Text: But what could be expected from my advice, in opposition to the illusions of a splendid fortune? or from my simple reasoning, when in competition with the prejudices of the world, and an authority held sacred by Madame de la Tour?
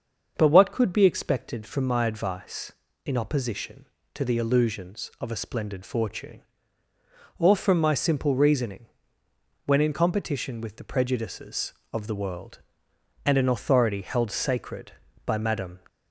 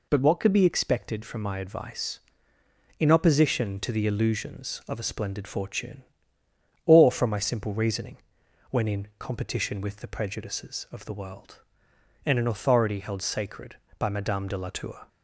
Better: second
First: starts louder than the rest; until 1.3 s; 6.5 dB // stops before "de la Tour"; at 15.8 s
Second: none

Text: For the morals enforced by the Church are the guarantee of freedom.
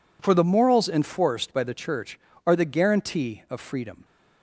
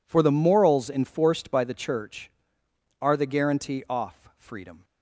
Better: first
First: none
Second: says "off" for "of"; at 3.8 s

